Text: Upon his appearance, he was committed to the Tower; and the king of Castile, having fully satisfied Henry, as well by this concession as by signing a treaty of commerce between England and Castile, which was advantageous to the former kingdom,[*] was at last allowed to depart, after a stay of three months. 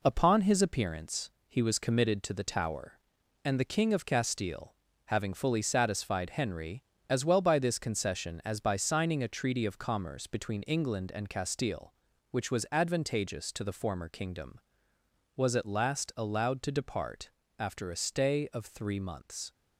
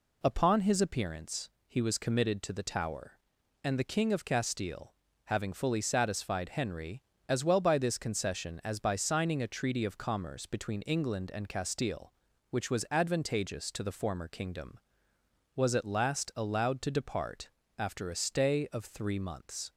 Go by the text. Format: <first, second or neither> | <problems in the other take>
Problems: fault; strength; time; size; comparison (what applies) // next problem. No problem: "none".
second | gets quieter; strong; throughout; 7 dB